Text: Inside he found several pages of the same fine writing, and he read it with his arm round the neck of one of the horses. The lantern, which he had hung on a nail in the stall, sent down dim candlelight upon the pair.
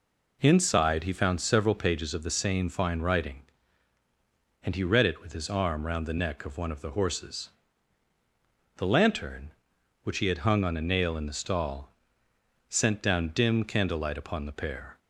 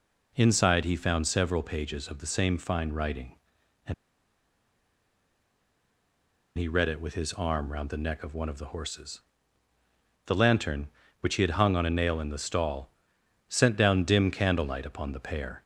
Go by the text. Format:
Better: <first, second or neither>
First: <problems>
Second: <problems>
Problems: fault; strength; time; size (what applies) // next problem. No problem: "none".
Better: first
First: none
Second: pauses between "and" and "he"; strong; at 3.9 s; 2.6 s long